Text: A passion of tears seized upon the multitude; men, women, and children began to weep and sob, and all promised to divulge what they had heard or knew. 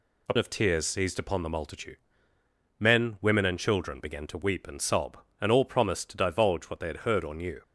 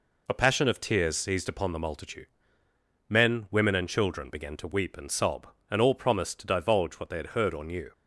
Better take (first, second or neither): second